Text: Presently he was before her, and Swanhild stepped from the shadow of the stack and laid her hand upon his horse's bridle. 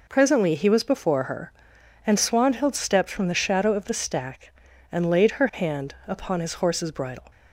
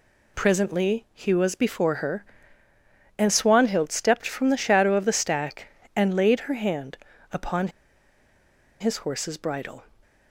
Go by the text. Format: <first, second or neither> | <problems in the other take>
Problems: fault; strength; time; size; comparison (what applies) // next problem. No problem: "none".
first | pauses between "hand" and "upon"; slight; at 6.9 s; 0.34 s long // pauses between "upon" and "his"; at 7.6 s; 1.1 s long